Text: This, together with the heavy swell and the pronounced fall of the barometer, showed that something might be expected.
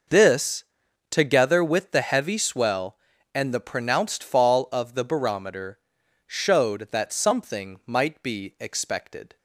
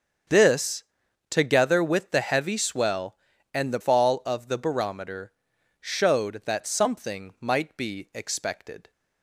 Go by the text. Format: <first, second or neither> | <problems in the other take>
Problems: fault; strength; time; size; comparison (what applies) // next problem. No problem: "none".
first | starts louder than the rest; strong; until 1.7 s; 7.5 dB // skips "pronounced"; at 3.7 s